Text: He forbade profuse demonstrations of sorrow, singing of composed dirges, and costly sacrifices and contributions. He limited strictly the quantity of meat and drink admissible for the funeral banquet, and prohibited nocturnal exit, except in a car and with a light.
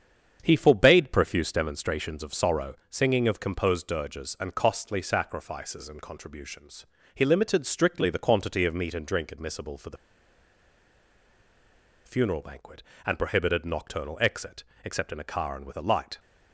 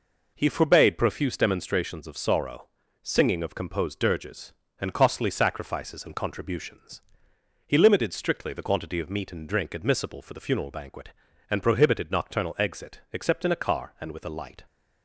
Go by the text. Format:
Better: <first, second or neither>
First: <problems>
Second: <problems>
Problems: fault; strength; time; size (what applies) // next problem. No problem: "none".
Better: second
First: starts louder than the rest; strong; until 1.4 s; 7.5 dB // pauses between "the" and "funeral"; strong; at 9.9 s; 2.1 s long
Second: none